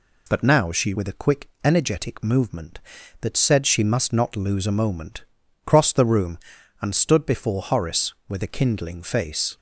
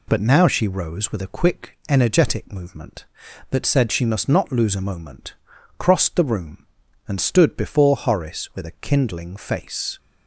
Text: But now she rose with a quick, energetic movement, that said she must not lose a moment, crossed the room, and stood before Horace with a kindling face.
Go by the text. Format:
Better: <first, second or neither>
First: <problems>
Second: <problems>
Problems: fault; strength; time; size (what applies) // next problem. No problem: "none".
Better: second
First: skips "rose"; at 0.9 s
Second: none